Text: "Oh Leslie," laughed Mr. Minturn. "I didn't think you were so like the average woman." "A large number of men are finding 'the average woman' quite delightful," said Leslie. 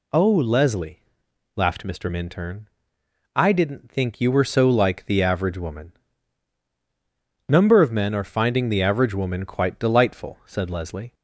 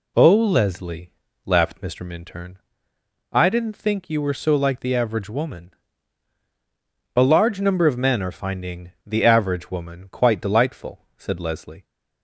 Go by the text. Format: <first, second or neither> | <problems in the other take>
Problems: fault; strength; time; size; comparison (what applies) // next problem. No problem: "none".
second | skips "A large"; at 6.7 s